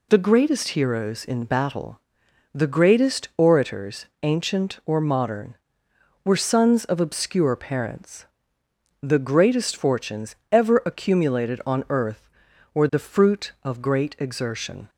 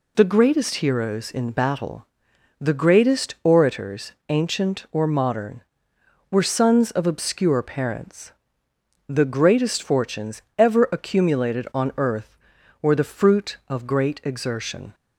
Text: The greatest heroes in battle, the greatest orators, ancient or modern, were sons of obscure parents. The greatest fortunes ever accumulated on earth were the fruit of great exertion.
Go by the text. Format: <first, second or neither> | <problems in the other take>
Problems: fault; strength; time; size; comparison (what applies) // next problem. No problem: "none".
neither | pauses between "fortunes" and "ever"; slight; the same in both